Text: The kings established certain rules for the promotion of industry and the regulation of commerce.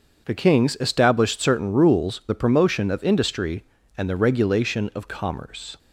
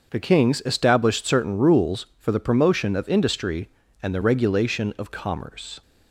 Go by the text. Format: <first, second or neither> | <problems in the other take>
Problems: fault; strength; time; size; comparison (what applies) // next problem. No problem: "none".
second | starts louder than the rest; until 1.3 s; 6.5 dB; also in the second // skips "for"; at 2.2 s